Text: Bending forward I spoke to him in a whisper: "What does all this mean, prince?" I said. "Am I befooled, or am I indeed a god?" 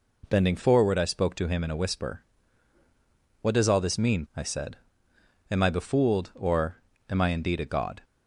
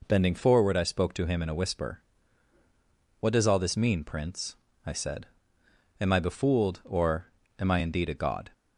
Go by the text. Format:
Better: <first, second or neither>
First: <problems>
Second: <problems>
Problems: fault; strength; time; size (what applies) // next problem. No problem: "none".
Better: second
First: skips "prince"; at 4.2 s // pauses between "or" and "am"; slight; at 6.8 s; 0.26 s long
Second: pauses between "or" and "am"; slight; at 7.3 s; 0.26 s long